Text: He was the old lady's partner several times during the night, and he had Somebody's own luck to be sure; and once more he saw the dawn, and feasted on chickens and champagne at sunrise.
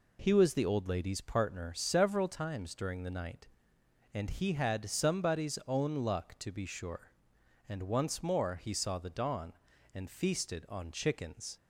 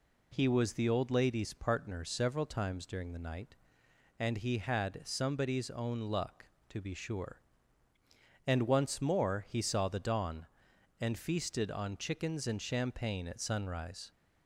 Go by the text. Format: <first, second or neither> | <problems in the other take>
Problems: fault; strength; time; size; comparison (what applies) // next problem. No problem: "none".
second | stops before "and champagne at sunrise"; at 11.5 s